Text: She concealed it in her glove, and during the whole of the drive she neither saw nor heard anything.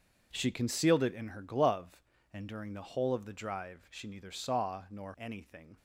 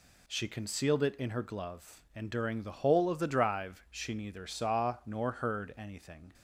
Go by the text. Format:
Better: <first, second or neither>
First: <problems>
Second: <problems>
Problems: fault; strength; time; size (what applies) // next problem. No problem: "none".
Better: second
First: skips "heard"; at 5.1 s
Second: none